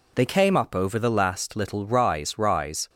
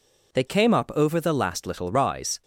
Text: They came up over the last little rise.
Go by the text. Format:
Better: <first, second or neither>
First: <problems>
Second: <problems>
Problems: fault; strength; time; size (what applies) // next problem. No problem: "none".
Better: second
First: says "rise" twice; at 2.3 s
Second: none